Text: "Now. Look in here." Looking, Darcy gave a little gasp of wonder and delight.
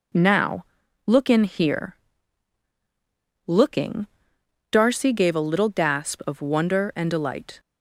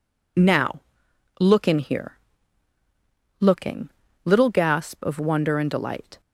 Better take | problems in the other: first | skips "Darcy gave a"; at 4.0 s

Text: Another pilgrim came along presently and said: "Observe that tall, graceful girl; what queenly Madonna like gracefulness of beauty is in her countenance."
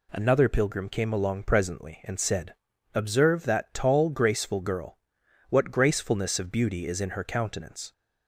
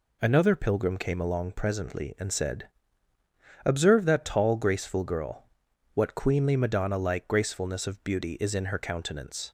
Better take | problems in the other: second | skips "queenly Madonna like"; at 5.6 s

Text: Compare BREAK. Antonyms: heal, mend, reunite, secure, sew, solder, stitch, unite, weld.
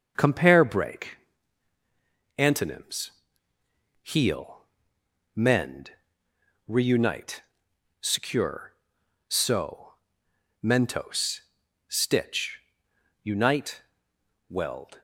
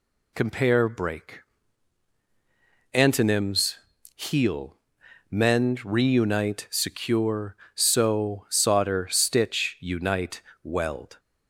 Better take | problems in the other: second | starts louder than the rest; until 1.1 s; 6 dB // says "mentos" for "solder"; at 10.6 s

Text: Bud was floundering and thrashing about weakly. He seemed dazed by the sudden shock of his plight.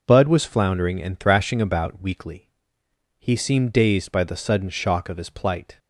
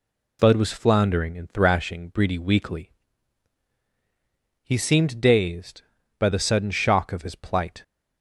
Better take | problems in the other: first | says "breedy" for "about"; at 2.0 s

